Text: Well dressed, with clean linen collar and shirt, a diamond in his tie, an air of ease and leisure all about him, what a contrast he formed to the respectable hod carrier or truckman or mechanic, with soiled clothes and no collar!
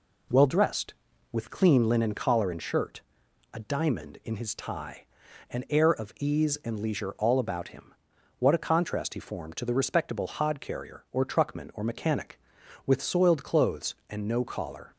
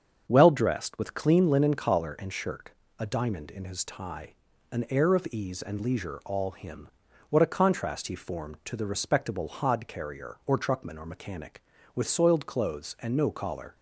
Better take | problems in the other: first | starts louder than the rest; strong; until 1.2 s; 7 dB // skips "about"; at 6.5 s

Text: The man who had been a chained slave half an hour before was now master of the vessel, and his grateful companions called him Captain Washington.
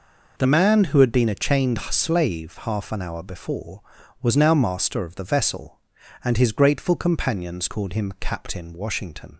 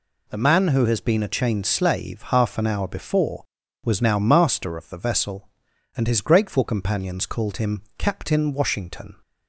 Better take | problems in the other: first | says "has" for "had"; at 0.8 s // pauses between "him" and "Captain"; slight; at 7.8 s; 0.16 s long

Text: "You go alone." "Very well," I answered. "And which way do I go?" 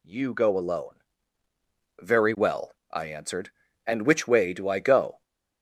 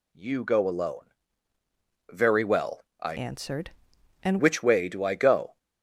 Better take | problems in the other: first | changes voice from "answered" to "And"; from 3.1 to 4.3 s; 1.2 s long

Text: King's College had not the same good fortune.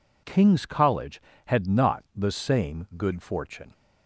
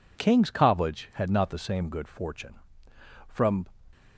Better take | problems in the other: first | goes on to say "From"; slight; from 3.2 s on; 0.38 s long

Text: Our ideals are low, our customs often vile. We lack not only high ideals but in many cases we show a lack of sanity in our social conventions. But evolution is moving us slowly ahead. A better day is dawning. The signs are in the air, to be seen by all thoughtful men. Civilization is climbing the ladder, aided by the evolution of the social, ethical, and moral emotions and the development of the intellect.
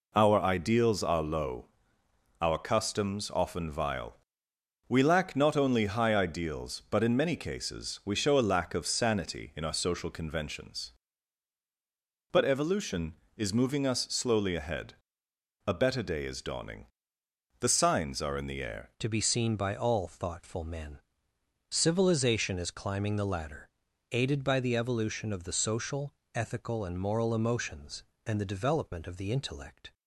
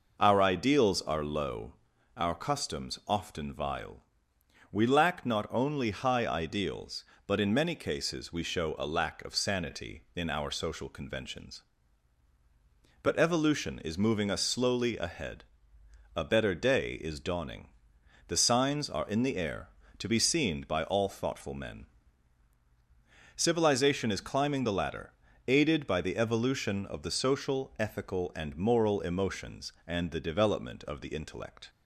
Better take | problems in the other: second | changes voice at "to"; from 18.9 s on; 11.0 s long

